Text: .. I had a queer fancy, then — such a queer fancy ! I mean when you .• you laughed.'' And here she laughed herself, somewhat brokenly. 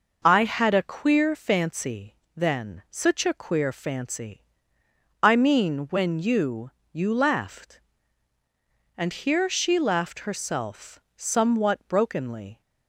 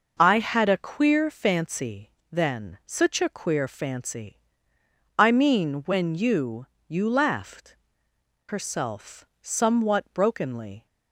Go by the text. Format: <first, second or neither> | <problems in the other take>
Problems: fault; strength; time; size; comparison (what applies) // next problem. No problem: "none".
first | skips "And here she laughed"; at 8.1 s